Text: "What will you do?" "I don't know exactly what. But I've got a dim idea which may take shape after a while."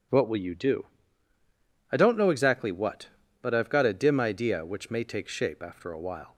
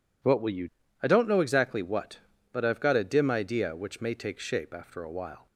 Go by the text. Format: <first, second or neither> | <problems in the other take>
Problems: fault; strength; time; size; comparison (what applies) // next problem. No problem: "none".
first | skips "do"; at 0.8 s